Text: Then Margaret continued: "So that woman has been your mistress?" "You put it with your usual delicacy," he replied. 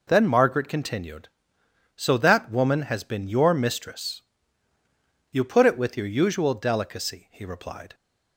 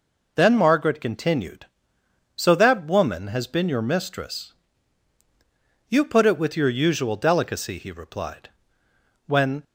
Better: first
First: none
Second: goes on to say "When"; slight; from 9.2 s on; 0.38 s long

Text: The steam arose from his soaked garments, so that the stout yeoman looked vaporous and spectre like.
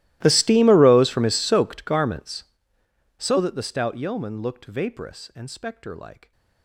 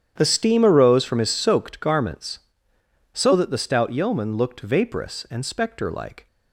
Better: second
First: gets quieter; strong; throughout; 28 dB // starts louder than the rest; strong; until 1.2 s; 17 dB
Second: starts louder than the rest; strong; until 1.1 s; 9 dB

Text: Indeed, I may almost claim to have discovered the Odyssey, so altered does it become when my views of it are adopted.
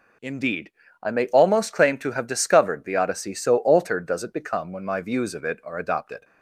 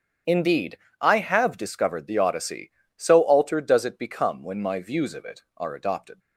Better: first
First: none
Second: starts louder than the rest; strong; until 1.4 s; 8 dB // skips "may almost claim to"; at 1.1 s

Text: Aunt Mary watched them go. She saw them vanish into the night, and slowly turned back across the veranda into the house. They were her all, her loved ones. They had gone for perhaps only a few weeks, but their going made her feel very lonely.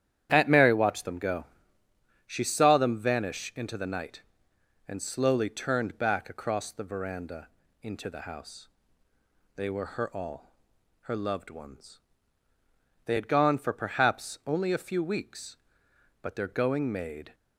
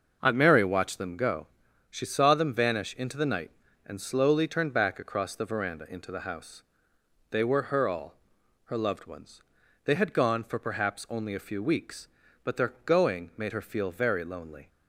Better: second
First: starts louder than the rest; strong; until 1.3 s; 10 dB // pauses between "veranda" and "into"; slight; at 7.4 s; 0.34 s long // stops before "her feel very lonely"; at 17.3 s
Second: starts louder than the rest; noticeable; until 1.2 s; 6 dB

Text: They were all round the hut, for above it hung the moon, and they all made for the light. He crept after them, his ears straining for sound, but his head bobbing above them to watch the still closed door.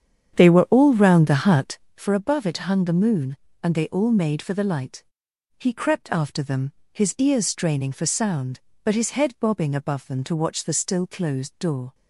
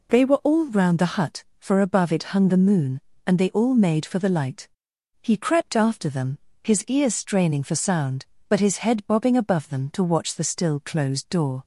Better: second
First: starts louder than the rest; strong; until 2.0 s; 8.5 dB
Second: none

